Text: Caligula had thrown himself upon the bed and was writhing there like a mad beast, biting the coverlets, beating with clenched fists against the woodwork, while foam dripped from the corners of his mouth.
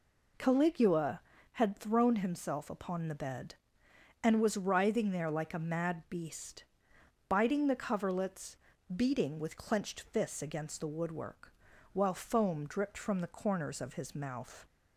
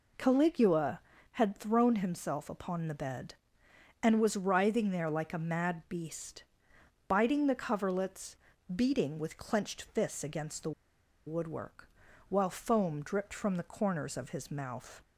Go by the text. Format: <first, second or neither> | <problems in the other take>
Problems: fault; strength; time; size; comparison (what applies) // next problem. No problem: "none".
first | pauses between "the" and "woodwork"; noticeable; at 10.7 s; 0.55 s long